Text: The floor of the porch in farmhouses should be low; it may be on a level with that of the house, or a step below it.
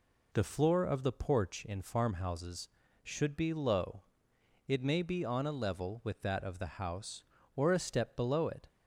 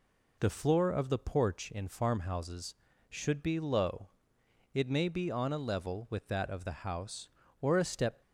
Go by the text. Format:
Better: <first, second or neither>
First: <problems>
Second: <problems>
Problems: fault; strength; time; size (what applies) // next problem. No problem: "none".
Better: first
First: none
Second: stops before "below it"; at 8.2 s